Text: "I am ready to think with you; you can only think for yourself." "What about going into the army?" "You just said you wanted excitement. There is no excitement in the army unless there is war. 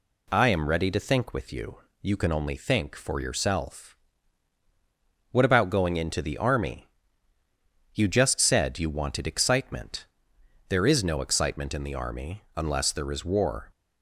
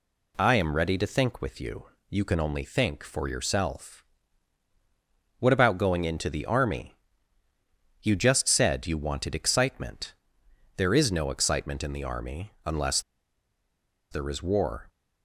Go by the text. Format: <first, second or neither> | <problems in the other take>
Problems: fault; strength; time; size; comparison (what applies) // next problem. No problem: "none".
first | pauses between "unless" and "there"; at 12.9 s; 1.1 s long